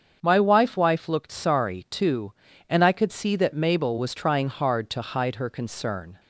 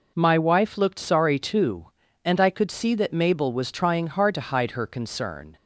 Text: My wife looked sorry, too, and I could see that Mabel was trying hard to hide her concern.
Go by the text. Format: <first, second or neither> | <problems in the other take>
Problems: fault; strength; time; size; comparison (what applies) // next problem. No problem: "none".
second | starts louder than the rest; strong; until 1.2 s; 7 dB // says "wife" twice; at 0.7 s